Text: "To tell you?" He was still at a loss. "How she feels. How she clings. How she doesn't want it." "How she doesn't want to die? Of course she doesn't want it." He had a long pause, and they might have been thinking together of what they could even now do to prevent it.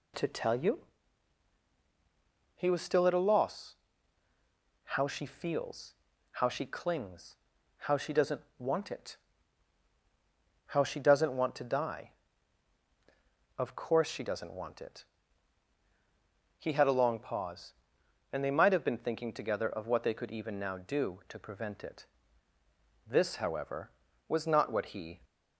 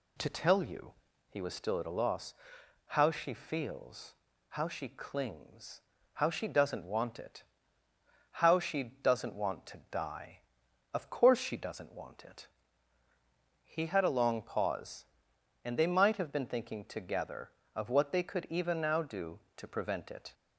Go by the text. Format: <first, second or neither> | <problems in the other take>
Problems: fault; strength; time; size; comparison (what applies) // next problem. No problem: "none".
second | pauses between "doesn't" and "want"; slight; at 8.4 s; 0.16 s long // goes on to say "This however was not what he"; strong; from 23.0 s on; 2.1 s long